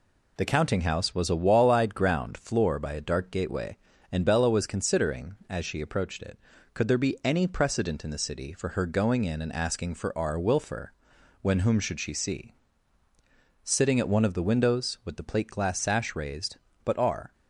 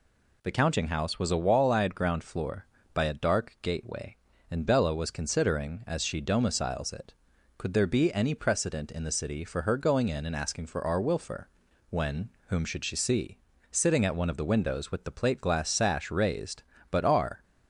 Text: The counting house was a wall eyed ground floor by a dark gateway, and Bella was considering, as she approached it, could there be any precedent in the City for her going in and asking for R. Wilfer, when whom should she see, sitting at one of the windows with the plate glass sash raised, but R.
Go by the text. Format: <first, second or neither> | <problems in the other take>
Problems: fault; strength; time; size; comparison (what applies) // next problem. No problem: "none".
first | says "domiciles" for "approached"; at 6.2 s // pauses between "when" and "whom"; slight; at 12.2 s; 0.18 s long